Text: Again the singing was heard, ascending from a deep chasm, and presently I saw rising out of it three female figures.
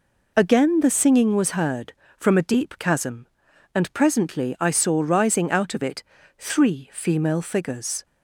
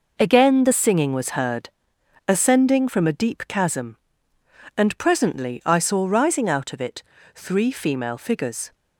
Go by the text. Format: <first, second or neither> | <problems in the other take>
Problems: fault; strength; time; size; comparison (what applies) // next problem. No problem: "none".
second | skips "ascending"; at 2.0 s // pauses between "it" and "three"; slight; at 6.0 s; 0.34 s long; slight in the second